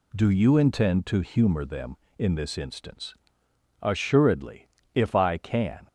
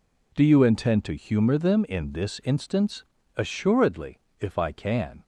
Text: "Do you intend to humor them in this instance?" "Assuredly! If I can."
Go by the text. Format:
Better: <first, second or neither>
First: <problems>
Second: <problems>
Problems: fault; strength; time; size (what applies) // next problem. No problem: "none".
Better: neither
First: none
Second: none